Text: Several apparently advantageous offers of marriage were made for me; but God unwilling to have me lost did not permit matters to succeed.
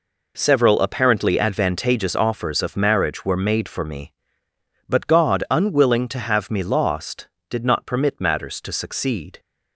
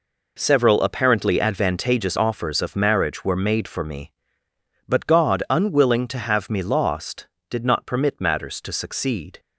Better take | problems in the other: neither | none

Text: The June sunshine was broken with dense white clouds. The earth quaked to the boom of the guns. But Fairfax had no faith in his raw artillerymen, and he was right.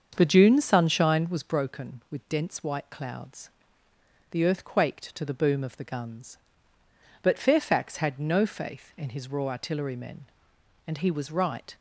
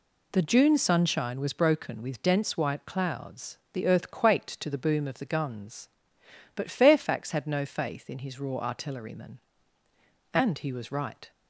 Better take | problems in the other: second | starts louder than the rest; until 1.7 s; 7 dB

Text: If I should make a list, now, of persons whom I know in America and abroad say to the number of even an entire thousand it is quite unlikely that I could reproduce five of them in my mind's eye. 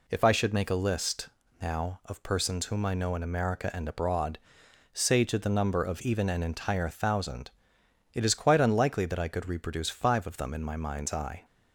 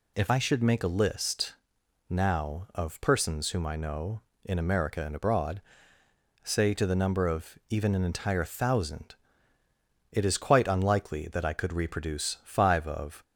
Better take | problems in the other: first | pauses between "abroad" and "say"; noticeable; at 5.6 s; 0.82 s long; noticeable in the first // pauses between "thousand" and "it"; noticeable; at 9.1 s; 0.96 s long; noticeable in the first // stops before "them in my mind's eye"; at 13.2 s

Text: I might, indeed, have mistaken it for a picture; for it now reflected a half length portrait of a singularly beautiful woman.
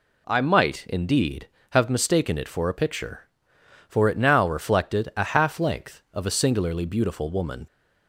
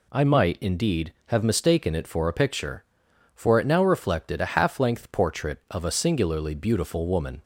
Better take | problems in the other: second | skips "portrait"; at 6.0 s

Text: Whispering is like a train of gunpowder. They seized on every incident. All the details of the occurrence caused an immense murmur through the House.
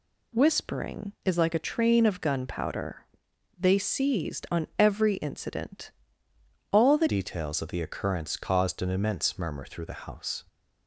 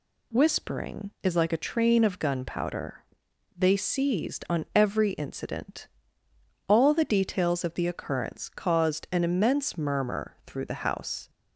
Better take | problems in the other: second | changes voice at "details"; from 7.0 s on; 3.4 s long

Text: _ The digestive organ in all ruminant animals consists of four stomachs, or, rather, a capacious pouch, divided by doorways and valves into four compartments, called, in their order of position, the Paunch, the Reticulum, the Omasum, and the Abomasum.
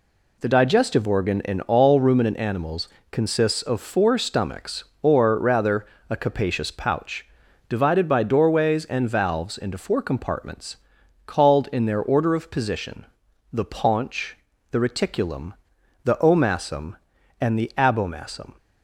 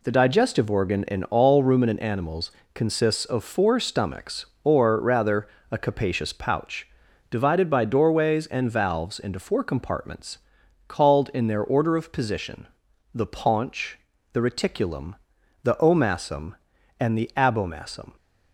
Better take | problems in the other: neither | pauses between "animals" and "consists"; slight; the same in both

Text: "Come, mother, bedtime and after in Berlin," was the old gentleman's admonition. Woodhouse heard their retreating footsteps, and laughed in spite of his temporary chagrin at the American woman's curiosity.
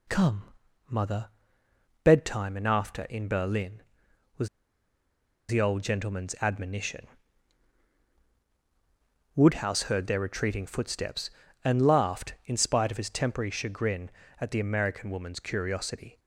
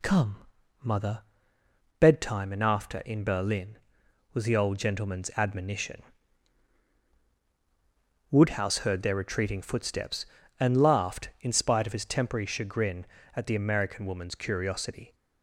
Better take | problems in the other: second | pauses between "was" and "the"; at 4.4 s; 1.0 s long

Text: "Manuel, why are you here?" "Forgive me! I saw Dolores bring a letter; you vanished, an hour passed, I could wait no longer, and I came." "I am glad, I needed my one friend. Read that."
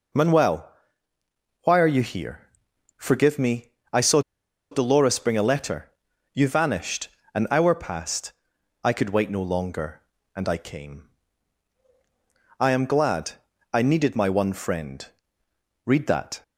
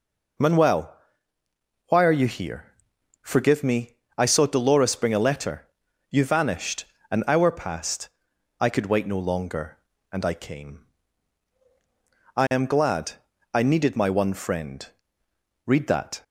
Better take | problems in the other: second | pauses between "saw" and "Dolores"; noticeable; at 4.2 s; 0.51 s long

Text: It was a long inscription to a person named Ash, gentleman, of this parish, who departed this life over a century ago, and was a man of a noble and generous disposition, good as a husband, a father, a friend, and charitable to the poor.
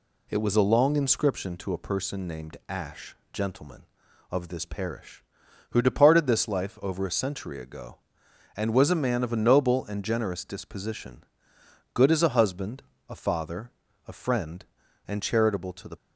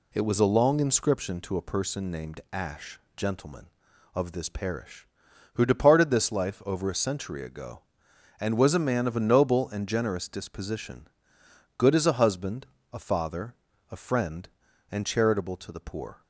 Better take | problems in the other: second | stops before "poor"; at 15.9 s

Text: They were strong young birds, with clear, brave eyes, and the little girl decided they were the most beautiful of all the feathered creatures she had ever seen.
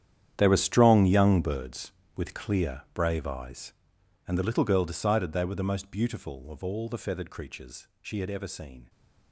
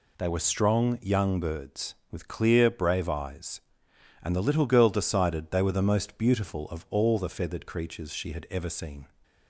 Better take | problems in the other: second | gets quieter; strong; throughout; 16 dB

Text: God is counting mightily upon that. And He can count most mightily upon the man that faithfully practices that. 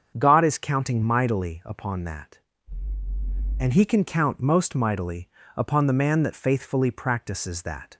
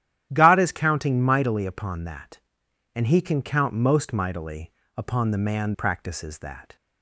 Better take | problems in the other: first | starts louder than the rest; strong; until 1.3 s; 12 dB; strong in the first // pauses between "mightily" and "upon"; slight; at 4.7 s; 0.26 s long; slight in the first // skips "that faithfully"; at 5.7 s

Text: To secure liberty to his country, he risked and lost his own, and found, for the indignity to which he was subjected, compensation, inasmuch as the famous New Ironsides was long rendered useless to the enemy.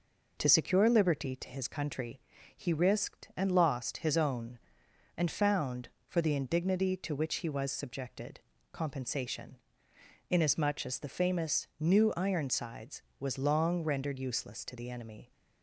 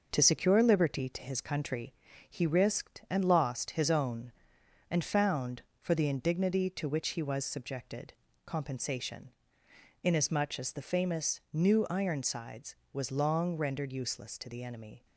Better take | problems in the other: first | gets quieter; noticeable; throughout; 4.5 dB

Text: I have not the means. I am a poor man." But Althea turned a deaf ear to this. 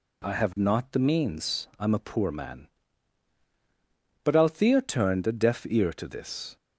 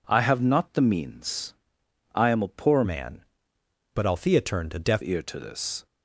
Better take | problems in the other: first | changes voice from "man" to "deaf"; from 2.8 to 5.0 s; 2.2 s long

